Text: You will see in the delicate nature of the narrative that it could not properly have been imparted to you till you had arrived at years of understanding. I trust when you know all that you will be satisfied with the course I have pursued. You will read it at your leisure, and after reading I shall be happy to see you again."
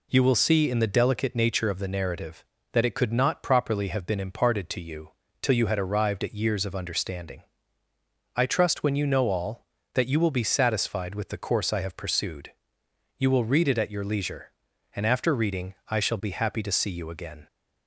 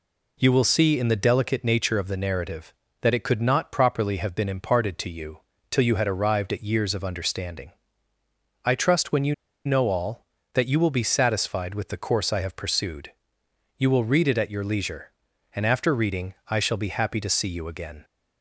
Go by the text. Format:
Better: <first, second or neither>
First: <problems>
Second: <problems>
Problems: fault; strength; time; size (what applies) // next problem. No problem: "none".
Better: first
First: pauses between "you" and "till"; slight; at 5.1 s; 0.32 s long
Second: pauses between "you" and "till"; slight; at 5.3 s; 0.32 s long // pauses between "you" and "know"; slight; at 9.3 s; 0.31 s long